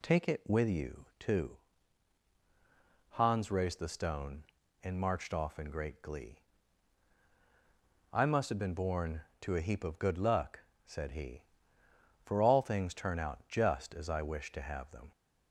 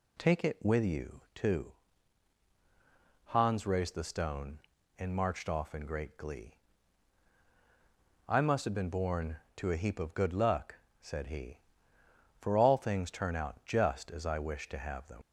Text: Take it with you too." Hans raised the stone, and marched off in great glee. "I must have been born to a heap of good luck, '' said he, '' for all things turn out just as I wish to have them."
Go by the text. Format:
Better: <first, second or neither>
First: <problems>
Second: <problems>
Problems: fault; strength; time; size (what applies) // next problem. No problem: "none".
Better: first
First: none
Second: leaves "them" unfinished; at 15.2 s; 65 ms